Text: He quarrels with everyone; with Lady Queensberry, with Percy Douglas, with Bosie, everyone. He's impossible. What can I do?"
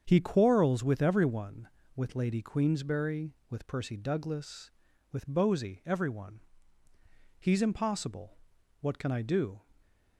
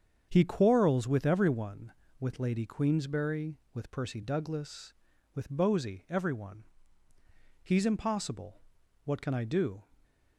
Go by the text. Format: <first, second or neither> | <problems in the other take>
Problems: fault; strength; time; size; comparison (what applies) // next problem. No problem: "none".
neither | starts louder than the rest; strong; the same in both